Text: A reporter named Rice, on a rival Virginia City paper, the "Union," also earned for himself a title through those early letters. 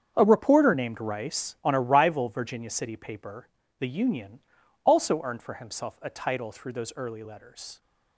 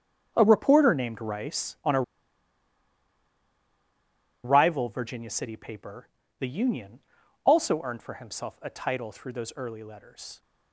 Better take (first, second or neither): first